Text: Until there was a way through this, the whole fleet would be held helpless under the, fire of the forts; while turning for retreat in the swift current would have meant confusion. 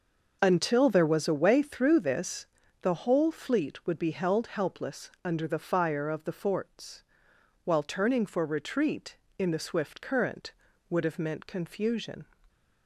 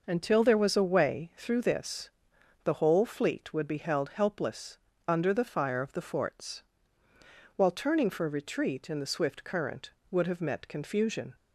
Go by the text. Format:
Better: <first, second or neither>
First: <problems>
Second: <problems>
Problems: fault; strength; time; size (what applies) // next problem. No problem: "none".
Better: first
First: none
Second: pauses between "helpless" and "under"; slight; at 4.7 s; 0.30 s long // says "met" for "meant"; at 10.4 s